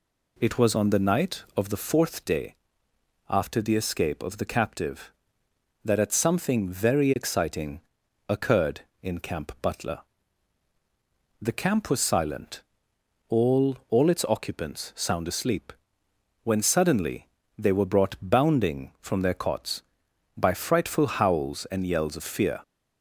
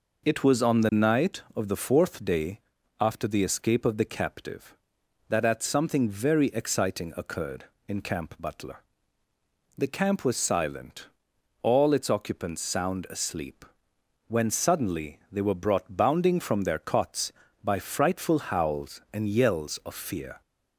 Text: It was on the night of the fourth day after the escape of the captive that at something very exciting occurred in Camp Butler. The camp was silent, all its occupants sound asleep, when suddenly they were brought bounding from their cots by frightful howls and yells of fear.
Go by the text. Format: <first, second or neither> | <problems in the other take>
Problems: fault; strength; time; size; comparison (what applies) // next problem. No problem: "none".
second | pauses between "day" and "after"; noticeable; at 2.5 s; 0.72 s long; also in the second // pauses between "exciting" and "occurred"; noticeable; at 7.8 s; 0.48 s long // says "all" twice; at 13.8 s // pauses between "suddenly" and "they"; slight; at 17.2 s; 0.30 s long